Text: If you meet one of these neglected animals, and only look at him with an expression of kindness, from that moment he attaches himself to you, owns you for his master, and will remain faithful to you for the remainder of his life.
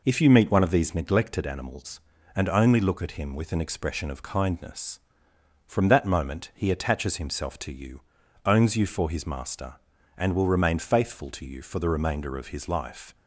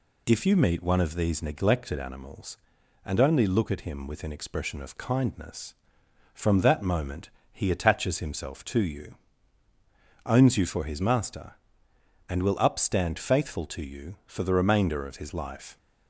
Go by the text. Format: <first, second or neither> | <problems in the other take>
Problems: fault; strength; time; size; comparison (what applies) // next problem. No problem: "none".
first | pauses between "moment" and "he"; slight; at 7.3 s; 0.20 s long // says "upstand" for "remain"; at 12.5 s